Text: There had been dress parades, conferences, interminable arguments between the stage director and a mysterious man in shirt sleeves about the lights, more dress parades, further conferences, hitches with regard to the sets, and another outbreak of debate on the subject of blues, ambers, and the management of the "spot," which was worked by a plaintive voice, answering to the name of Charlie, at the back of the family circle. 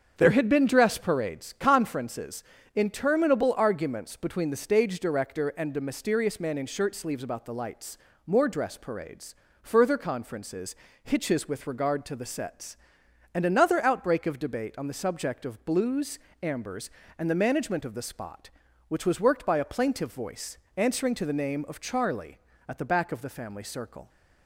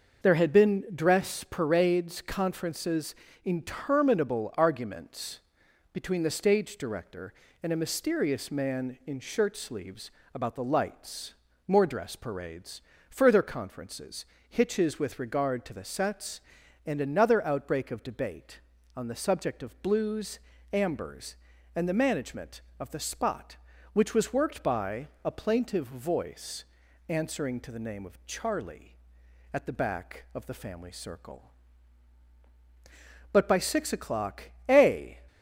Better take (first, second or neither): first